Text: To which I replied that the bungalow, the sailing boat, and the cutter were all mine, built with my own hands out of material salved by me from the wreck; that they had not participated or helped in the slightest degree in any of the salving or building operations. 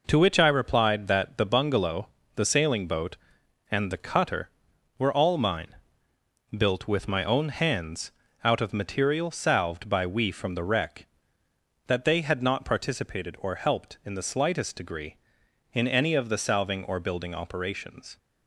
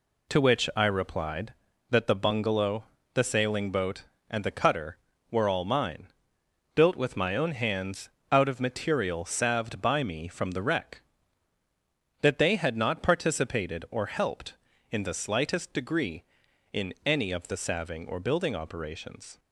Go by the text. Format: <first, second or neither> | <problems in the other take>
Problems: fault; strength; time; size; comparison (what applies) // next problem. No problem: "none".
second | pauses between "hands" and "out"; slight; at 8.1 s; 0.32 s long; slight in the second // says "we" for "me"; at 10.0 s